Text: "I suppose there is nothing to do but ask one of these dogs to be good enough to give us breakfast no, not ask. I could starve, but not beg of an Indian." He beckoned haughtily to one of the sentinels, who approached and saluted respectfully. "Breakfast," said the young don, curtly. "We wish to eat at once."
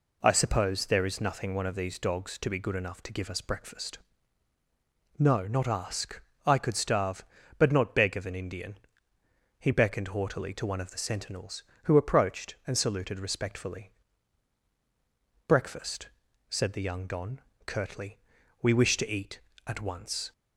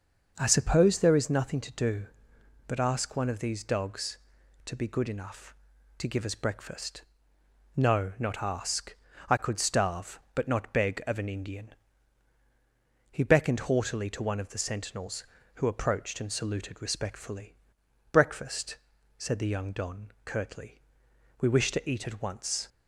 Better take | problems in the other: second | skips "to do but ask"; at 1.5 s // pauses between "breakfast" and "no"; at 3.9 s; 1.2 s long; noticeable in the second

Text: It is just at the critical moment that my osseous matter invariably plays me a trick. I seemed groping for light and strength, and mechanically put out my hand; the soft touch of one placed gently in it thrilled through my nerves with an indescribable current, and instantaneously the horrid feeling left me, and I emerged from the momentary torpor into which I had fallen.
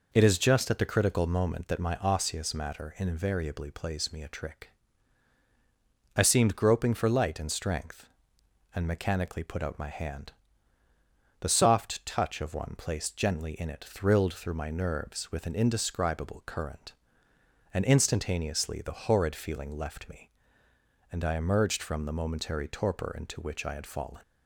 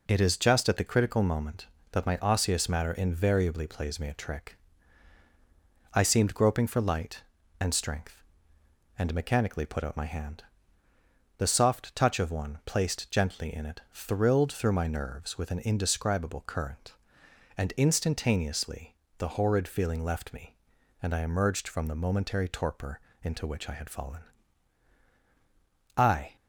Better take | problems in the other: first | pauses between "instantaneously" and "the"; slight; at 18.9 s; 0.24 s long // pauses between "torpor" and "into"; slight; at 22.9 s; 0.24 s long // goes on to say "I"; slight; from 25.9 s on; 0.38 s long

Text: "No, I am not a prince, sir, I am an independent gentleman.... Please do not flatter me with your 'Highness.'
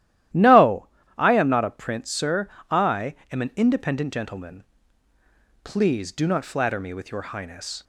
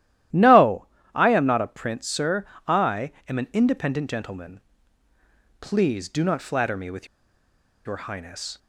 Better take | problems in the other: first | starts louder than the rest; strong; until 1.5 s; 13 dB; strong in the first // pauses between "I" and "am"; slight; at 3.1 s; 0.16 s long; slight in the first // pauses between "with" and "your"; noticeable; at 7.0 s; 0.79 s long

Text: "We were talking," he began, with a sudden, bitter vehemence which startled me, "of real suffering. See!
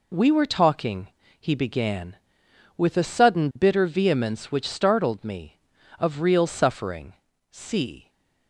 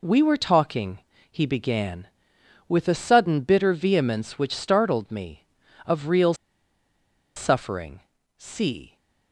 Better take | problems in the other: first | pauses between "real" and "suffering"; at 6.3 s; 1.0 s long

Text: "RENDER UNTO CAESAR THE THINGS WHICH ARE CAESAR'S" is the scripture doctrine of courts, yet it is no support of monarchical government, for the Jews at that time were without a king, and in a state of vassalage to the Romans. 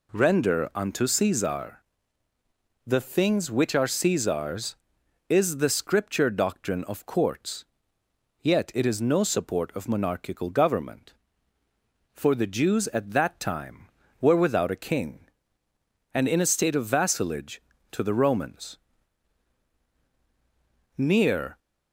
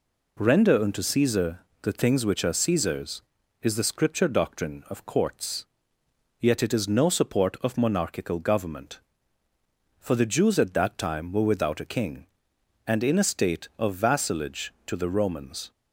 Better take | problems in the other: second | pauses between "CAESAR" and "THE"; at 1.8 s; 1.0 s long; slight in the second // goes on to say "Near"; noticeable; from 20.9 s on; 0.62 s long

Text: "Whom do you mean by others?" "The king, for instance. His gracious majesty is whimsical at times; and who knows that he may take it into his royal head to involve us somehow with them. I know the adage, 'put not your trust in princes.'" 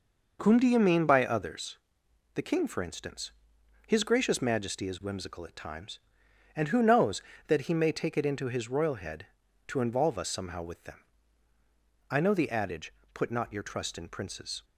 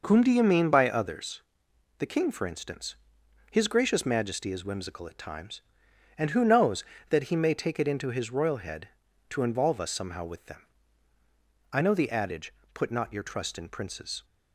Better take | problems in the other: neither | none

